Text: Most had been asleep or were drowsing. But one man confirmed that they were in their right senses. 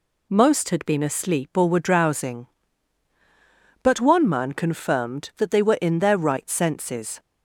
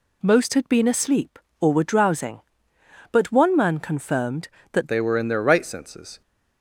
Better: first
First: none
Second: changes voice at "they"; from 4.8 s on; 1.4 s long

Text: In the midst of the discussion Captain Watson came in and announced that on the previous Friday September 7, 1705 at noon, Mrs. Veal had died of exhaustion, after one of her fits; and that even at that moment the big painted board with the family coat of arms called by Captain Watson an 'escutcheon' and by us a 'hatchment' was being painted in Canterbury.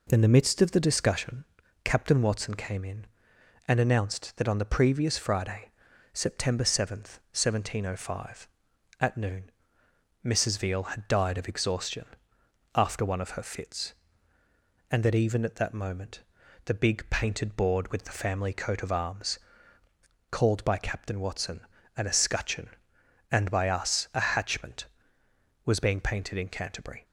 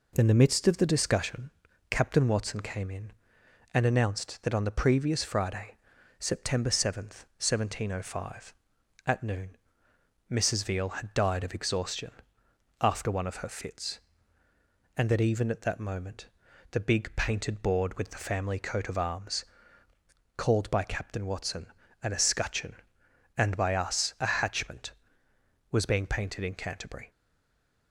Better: first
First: pauses between "discussion" and "Captain"; at 1.4 s; 0.40 s long // pauses between "Friday" and "September"; at 5.7 s; 0.44 s long // pauses between "moment" and "the"; at 16.2 s; 0.44 s long // pauses between "arms" and "called"; noticeable; at 19.3 s; 0.92 s long // pauses between "Watson" and "an"; at 21.6 s; 0.38 s long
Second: pauses between "discussion" and "Captain"; at 1.5 s; 0.40 s long // pauses between "Friday" and "September"; at 5.7 s; 0.44 s long // pauses between "moment" and "the"; at 16.2 s; 0.44 s long // pauses between "arms" and "called"; noticeable; at 19.4 s; 0.92 s long // pauses between "Watson" and "an"; at 21.6 s; 0.38 s long // stays silent after the last word; slight; from 27.1 s on; 0.8 s long

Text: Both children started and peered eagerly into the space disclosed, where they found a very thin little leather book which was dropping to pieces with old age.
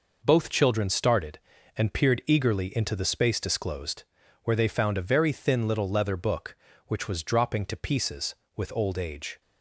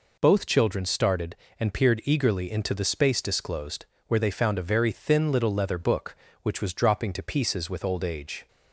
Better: neither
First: none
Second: none

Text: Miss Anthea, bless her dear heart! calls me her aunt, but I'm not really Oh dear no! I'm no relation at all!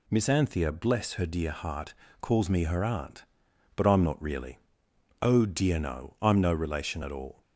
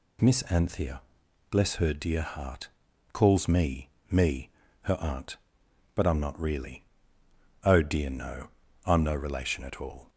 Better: first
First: pauses between "really" and "Oh"; noticeable; at 4.5 s; 0.62 s long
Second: says "me" twice; at 4.0 s // pauses between "really" and "Oh"; noticeable; at 6.8 s; 0.80 s long

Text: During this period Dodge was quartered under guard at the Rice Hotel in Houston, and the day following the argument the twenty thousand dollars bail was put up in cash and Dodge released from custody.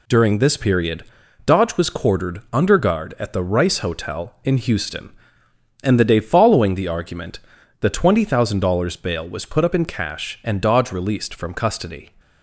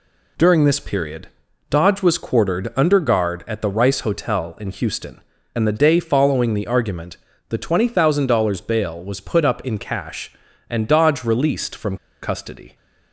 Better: first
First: pauses between "period" and "Dodge"; at 1.0 s; 0.40 s long // pauses between "argument" and "the"; at 7.3 s; 0.44 s long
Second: pauses between "period" and "Dodge"; at 1.2 s; 0.40 s long // pauses between "argument" and "the"; slight; at 7.1 s; 0.34 s long // pauses between "from" and "custody"; slight; at 11.9 s; 0.27 s long

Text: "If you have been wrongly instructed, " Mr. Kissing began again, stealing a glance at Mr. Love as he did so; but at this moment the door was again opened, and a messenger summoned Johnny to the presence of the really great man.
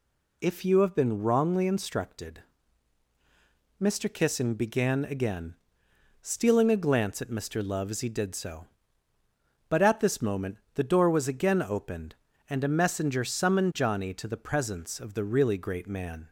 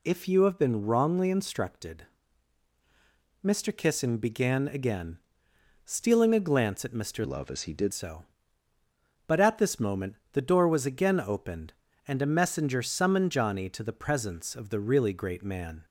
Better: first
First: pauses between "moment" and "the"; slight; at 10.5 s; 0.16 s long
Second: changes voice from "Love" to "did"; from 7.2 to 7.9 s; 0.7 s long // pauses between "moment" and "the"; slight; at 10.1 s; 0.16 s long

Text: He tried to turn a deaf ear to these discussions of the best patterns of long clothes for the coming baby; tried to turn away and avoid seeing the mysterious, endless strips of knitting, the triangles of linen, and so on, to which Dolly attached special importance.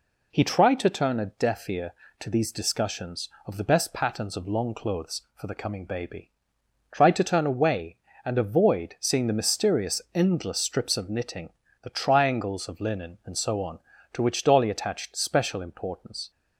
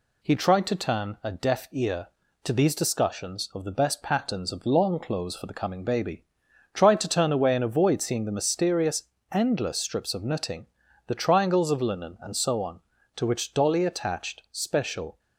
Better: first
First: none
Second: stops before "importance"; at 15.1 s

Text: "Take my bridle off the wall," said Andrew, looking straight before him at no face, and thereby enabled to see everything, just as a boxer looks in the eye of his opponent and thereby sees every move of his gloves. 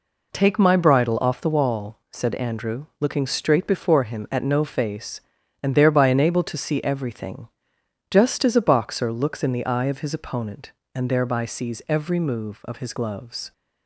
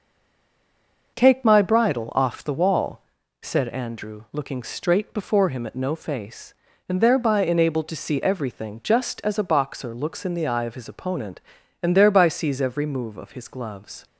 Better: first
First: none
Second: stays silent before the first word; until 1.1 s; 1.1 s long

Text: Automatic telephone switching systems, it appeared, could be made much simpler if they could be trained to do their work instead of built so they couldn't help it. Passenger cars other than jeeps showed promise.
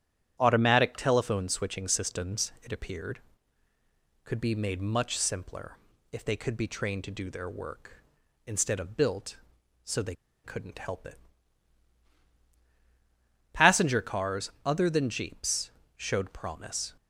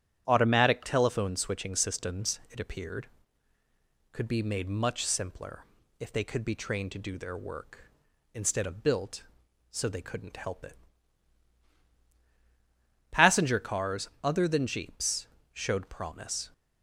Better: second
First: starts louder than the rest; strong; until 1.4 s; 10 dB // pauses between "simpler" and "if"; slight; at 5.7 s; 0.34 s long // pauses between "they" and "couldn't"; slight; at 10.1 s; 0.30 s long // pauses between "jeeps" and "showed"; slight; at 15.6 s; 0.26 s long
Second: starts louder than the rest; strong; until 1.2 s; 10 dB // pauses between "simpler" and "if"; slight; at 5.6 s; 0.34 s long // pauses between "jeeps" and "showed"; slight; at 15.2 s; 0.26 s long

